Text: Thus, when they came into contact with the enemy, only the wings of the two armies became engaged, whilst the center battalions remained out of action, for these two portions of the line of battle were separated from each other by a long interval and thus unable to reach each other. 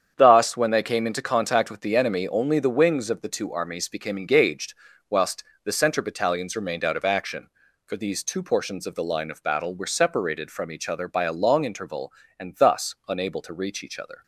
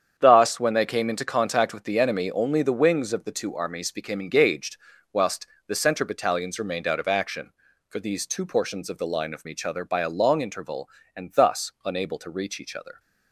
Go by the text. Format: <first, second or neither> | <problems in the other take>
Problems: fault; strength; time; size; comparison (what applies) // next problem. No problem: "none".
first | starts louder than the rest; strong; until 1.1 s; 8 dB; strong in the first // pauses between "whilst" and "the"; slight; at 5.4 s; 0.22 s long; slight in the first // skips "battle were separated from"; at 9.4 s